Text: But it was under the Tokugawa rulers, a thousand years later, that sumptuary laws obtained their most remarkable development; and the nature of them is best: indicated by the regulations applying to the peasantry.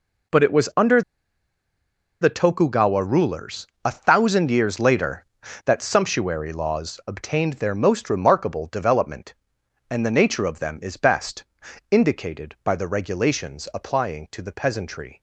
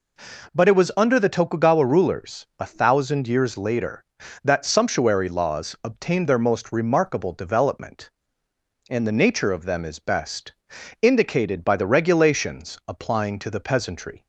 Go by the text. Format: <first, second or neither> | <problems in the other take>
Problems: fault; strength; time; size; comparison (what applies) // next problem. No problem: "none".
second | pauses between "under" and "the"; at 1.0 s; 1.1 s long